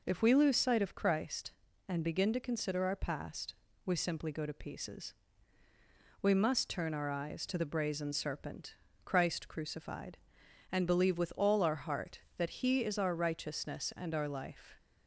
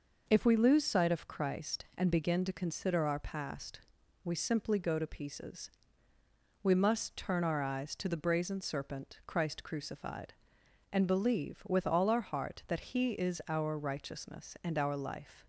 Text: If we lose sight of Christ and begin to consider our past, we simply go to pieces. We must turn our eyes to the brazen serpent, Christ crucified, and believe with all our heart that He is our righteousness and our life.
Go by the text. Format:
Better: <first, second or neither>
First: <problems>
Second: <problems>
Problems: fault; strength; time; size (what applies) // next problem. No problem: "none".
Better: neither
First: none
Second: none